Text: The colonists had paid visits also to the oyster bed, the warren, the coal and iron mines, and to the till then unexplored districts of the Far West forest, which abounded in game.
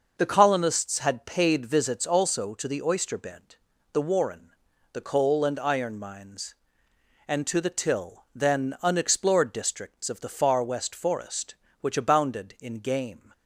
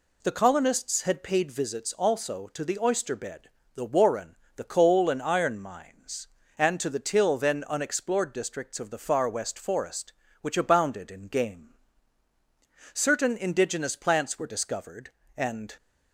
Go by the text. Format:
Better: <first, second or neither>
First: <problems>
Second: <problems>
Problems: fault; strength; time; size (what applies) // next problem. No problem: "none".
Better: first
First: none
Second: goes on to say "Certain indigenous plants were discovered and"; strong; from 12.9 s on; 2.8 s long